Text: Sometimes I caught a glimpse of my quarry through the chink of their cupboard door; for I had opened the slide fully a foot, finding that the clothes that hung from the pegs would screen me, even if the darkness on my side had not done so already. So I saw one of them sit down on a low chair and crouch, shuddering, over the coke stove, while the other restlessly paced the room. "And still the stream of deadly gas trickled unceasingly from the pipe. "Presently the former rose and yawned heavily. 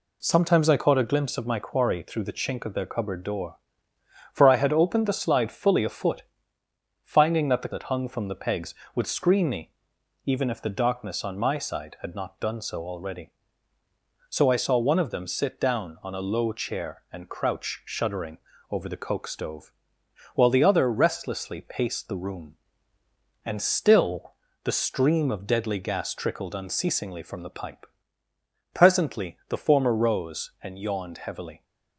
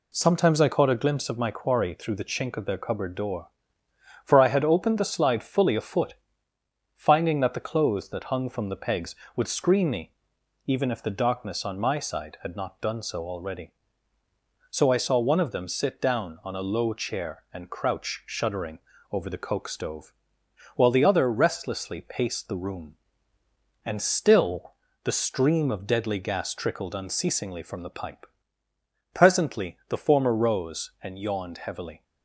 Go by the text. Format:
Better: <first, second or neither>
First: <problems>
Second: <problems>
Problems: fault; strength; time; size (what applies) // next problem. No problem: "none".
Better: second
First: skips "clothes"; at 7.7 s // pauses between "still" and "the"; slight; at 24.3 s; 0.32 s long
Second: pauses between "still" and "the"; slight; at 24.7 s; 0.32 s long